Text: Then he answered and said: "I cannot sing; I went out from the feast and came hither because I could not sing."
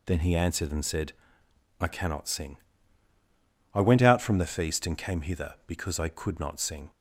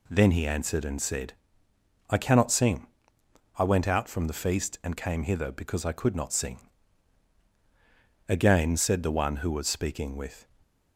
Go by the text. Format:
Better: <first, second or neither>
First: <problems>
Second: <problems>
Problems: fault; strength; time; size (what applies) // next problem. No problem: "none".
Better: first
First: none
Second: goes on to say "Again said the one who was speaking with"; strong; from 8.2 s on; 2.1 s long // stays silent after the last word; slight; from 10.4 s on; 0.5 s long